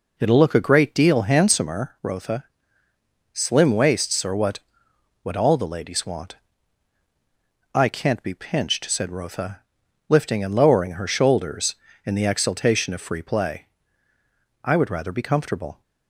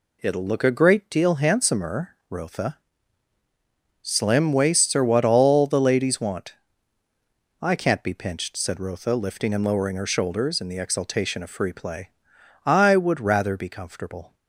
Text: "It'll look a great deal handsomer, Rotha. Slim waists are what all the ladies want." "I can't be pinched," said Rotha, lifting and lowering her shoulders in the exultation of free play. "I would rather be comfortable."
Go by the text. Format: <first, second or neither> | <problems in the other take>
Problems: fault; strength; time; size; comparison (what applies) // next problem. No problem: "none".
second | says "what" twice; at 5.2 s